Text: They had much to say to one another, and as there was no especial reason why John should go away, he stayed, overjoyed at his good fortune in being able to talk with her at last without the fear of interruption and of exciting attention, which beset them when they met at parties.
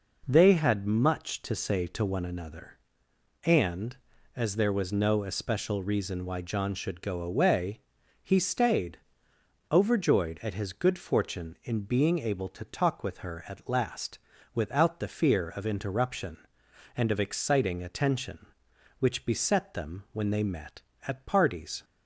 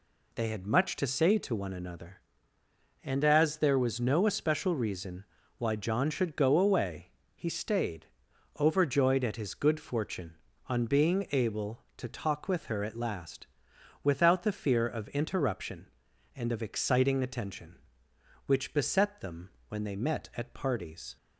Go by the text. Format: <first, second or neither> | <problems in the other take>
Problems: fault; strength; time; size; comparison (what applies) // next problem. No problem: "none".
first | pauses between "reason" and "why"; slight; at 5.2 s; 0.34 s long // says "on" for "in"; at 10.6 s // pauses between "last" and "without"; noticeable; at 13.4 s; 0.58 s long; slight in the first // pauses between "them" and "when"; slight; at 19.5 s; 0.18 s long